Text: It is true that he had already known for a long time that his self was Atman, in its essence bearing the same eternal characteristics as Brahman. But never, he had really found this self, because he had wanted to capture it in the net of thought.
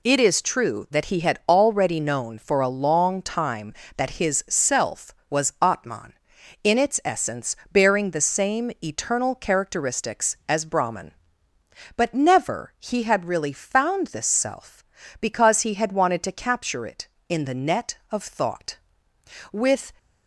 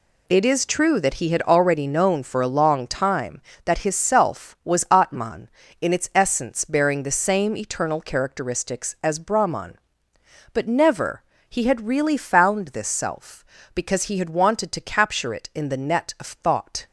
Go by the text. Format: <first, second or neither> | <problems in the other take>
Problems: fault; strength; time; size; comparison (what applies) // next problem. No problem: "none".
second | pauses between "essence" and "bearing"; slight; at 7.5 s; 0.16 s long // goes on to say "With"; slight; from 19.5 s on; 0.40 s long